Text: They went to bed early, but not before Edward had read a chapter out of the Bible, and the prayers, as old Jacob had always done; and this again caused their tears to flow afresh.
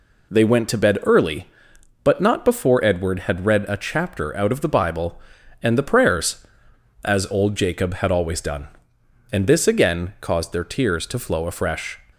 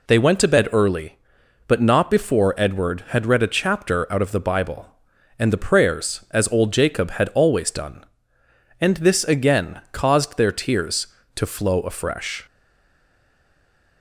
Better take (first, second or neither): first